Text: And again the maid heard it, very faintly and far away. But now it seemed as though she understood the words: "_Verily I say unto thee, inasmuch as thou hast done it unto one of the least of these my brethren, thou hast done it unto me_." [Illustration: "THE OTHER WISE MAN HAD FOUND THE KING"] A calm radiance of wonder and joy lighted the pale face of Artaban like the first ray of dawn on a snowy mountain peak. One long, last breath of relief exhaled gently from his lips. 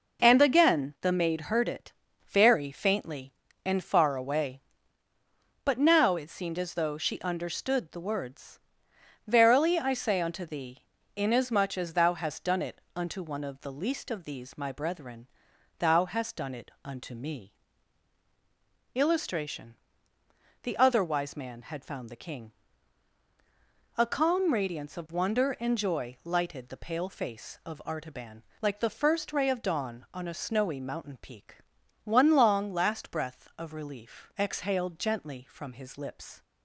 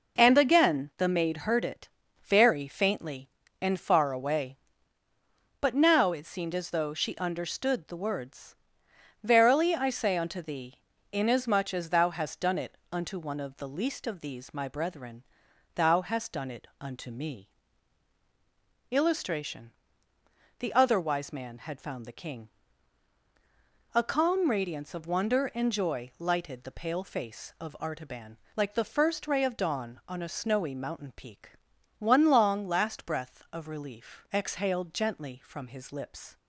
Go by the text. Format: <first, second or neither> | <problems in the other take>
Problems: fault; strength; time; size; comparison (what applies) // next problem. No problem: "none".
neither | pauses between "KING" and "A"; strong; the same in both // pauses between "Artaban" and "like"; slight; the same in both